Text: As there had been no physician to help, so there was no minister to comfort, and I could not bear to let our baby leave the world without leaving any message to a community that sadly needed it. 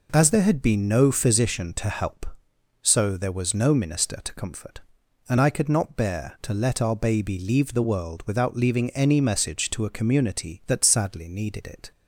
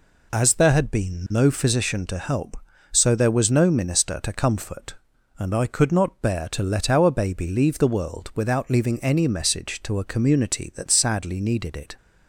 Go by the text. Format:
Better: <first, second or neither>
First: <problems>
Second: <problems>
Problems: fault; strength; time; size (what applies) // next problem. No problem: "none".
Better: neither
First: none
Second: none